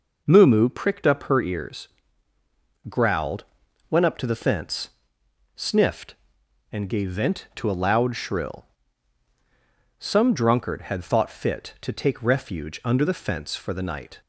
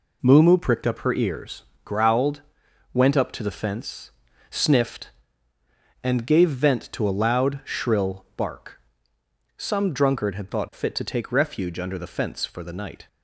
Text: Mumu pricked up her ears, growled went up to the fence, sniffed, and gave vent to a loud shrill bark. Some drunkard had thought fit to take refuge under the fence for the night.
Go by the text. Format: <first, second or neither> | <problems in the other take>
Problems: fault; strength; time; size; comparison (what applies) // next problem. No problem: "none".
second | pauses between "growled" and "went"; noticeable; at 3.4 s; 0.46 s long; noticeable in the second // skips "bark"; at 9.3 s